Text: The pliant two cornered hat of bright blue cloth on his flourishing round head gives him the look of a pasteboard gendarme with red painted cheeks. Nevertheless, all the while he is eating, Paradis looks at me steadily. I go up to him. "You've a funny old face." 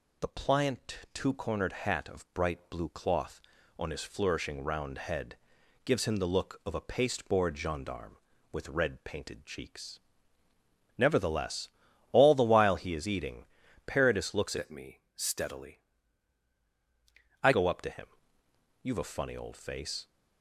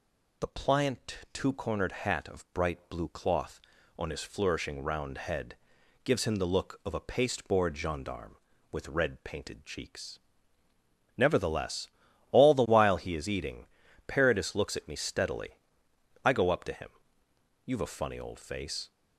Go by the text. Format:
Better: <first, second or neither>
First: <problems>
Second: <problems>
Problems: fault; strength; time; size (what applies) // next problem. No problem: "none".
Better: second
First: pauses between "head" and "gives"; noticeable; at 5.3 s; 0.48 s long // changes voice from "at" to "I"; from 14.5 to 17.5 s; 3.0 s long // pauses between "me" and "steadily"; slight; at 14.9 s; 0.16 s long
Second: pauses between "head" and "gives"; noticeable; at 5.5 s; 0.48 s long